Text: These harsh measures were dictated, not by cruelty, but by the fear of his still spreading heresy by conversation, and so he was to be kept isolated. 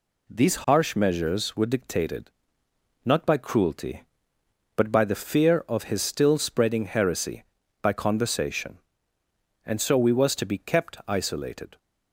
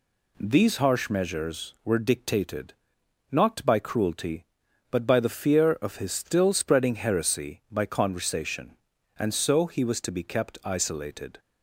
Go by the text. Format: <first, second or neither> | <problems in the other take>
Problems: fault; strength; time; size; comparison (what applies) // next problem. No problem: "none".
second | says "we" for "he"; at 9.9 s